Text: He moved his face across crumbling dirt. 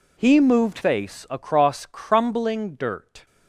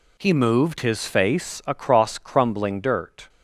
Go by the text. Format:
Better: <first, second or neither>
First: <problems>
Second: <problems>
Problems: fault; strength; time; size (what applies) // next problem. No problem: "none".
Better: second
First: skips "his"; at 0.8 s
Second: none